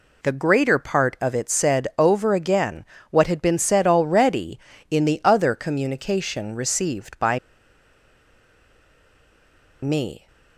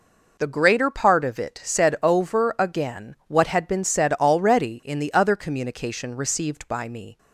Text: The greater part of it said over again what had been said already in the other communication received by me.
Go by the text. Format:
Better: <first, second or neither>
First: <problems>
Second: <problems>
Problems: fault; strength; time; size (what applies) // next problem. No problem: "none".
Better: second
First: pauses between "again" and "what"; slight; at 2.8 s; 0.24 s long // pauses between "by" and "me"; strong; at 7.3 s; 2.4 s long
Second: none